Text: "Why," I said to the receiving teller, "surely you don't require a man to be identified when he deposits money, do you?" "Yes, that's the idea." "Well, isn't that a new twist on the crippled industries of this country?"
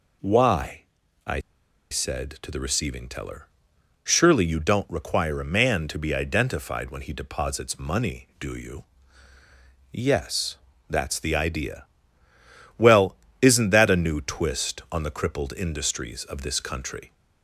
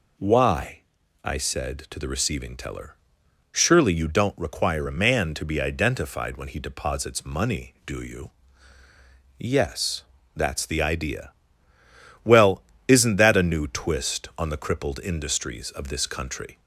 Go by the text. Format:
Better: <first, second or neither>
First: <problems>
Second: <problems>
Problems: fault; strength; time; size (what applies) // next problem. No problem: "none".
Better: second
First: pauses between "I" and "said"; noticeable; at 1.3 s; 0.51 s long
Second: none